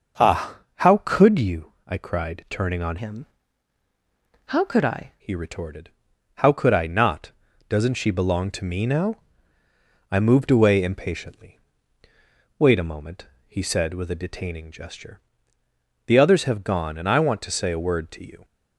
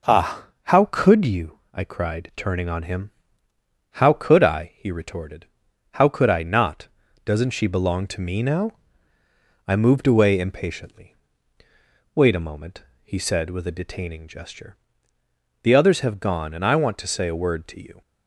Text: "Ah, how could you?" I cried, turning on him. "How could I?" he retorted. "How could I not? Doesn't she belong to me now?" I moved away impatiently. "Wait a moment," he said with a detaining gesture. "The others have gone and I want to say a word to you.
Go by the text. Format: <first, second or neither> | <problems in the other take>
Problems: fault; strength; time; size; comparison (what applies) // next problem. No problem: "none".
second | starts louder than the rest; noticeable; until 1.4 s; 6 dB // changes voice from "him" to "I"; from 2.9 to 5.1 s; 2.2 s long